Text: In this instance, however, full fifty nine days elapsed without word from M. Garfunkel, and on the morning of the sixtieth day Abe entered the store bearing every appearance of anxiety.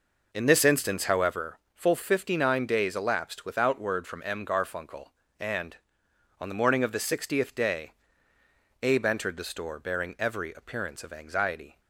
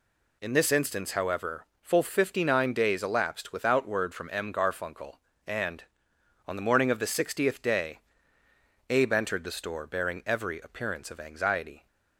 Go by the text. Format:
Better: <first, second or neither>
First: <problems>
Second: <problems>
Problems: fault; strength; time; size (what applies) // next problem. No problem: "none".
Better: second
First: starts louder than the rest; noticeable; until 1.4 s; 5 dB // pauses between "day" and "Abe"; noticeable; at 7.9 s; 0.90 s long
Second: pauses between "day" and "Abe"; noticeable; at 8.0 s; 0.90 s long